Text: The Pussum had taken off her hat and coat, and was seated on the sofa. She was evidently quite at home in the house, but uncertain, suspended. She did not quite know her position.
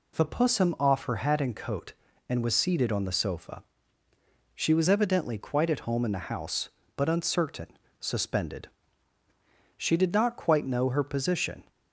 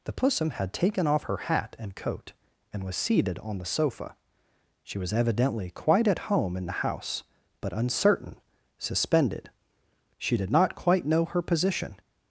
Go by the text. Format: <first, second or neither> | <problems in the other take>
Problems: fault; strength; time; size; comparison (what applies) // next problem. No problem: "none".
second | skips "had taken"; at 0.7 s